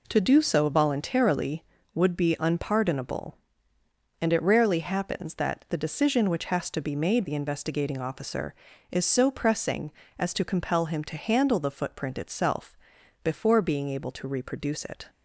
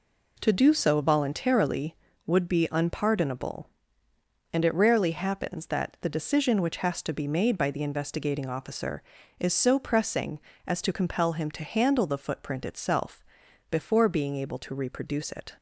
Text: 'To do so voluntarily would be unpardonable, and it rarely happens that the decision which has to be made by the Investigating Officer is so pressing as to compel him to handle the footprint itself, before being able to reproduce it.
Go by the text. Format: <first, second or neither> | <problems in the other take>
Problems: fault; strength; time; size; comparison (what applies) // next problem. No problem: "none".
second | skips "by"; at 7.2 s